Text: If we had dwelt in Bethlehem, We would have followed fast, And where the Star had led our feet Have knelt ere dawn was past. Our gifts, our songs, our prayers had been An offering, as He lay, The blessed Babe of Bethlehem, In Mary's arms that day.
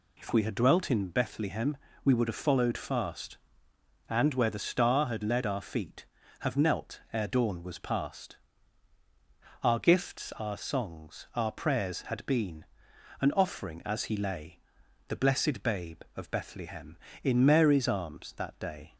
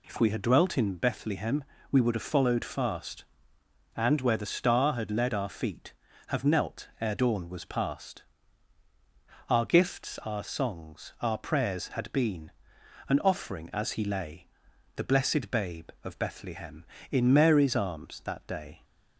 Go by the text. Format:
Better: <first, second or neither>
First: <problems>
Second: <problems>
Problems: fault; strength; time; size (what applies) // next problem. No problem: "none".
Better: neither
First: pauses between "been" and "An"; noticeable; at 12.6 s; 0.54 s long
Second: pauses between "been" and "An"; noticeable; at 12.5 s; 0.56 s long